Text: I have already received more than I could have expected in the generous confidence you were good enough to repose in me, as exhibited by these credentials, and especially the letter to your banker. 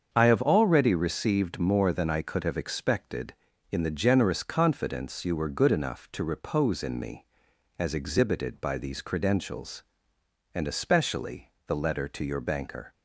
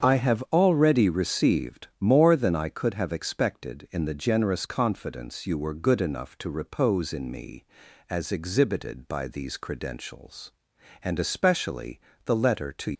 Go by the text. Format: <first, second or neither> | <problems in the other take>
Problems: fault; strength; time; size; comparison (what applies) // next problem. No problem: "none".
first | starts louder than the rest; strong; until 1.1 s; 7 dB; strong in the first // pauses between "especially" and "the"; slight; at 11.9 s; 0.28 s long; slight in the first // stops before "your banker"; at 12.9 s